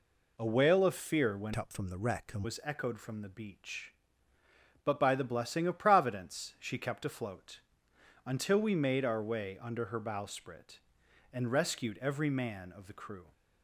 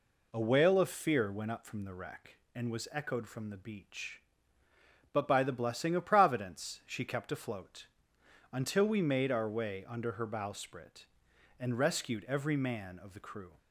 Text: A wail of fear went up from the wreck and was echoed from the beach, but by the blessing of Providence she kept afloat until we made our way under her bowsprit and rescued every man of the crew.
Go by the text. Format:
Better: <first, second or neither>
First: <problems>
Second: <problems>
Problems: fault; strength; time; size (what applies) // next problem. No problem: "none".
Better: second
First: changes voice from "up" to "and"; from 1.5 to 2.4 s; 0.9 s long // pauses between "afloat" and "until"; noticeable; at 7.5 s; 0.64 s long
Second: pauses between "afloat" and "until"; noticeable; at 7.8 s; 0.64 s long